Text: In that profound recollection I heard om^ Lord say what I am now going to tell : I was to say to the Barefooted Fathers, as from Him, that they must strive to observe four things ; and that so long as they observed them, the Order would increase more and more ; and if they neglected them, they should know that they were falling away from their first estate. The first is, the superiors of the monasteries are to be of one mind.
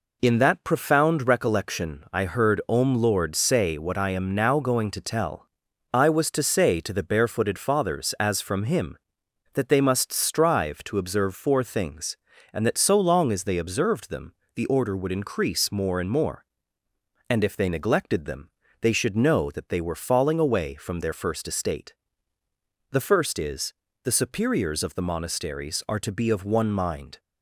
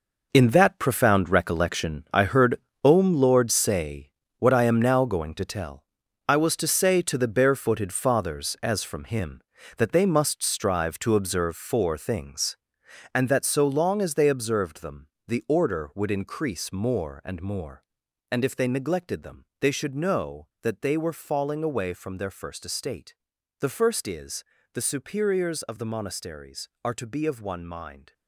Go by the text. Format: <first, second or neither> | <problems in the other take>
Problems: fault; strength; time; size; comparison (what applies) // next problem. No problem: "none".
first | gets quieter; strong; throughout; 11 dB // pauses between "heard" and "om"; slight; at 2.5 s; 0.24 s long // pauses between "say" and "what"; slight; at 4.1 s; 0.26 s long